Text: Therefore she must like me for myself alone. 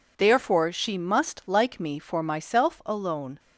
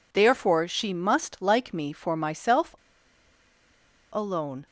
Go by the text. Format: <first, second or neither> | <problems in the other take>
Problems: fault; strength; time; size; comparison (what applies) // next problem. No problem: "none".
first | pauses between "myself" and "alone"; strong; at 2.7 s; 1.3 s long